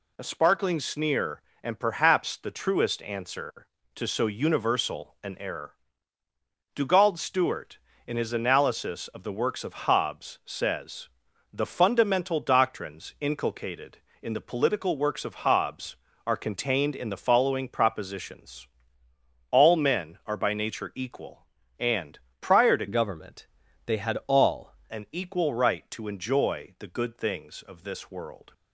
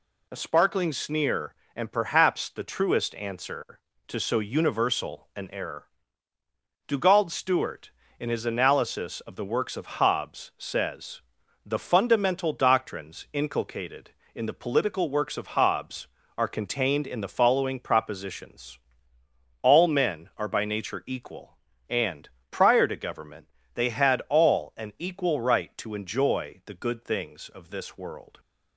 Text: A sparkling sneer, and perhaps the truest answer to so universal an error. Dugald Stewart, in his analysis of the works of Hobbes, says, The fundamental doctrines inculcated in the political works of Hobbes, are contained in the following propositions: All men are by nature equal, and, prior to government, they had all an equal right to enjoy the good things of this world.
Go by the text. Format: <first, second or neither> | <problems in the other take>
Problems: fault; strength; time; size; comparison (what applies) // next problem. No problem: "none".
second | changes voice from "government" to "all"; from 22.8 to 24.7 s; 1.9 s long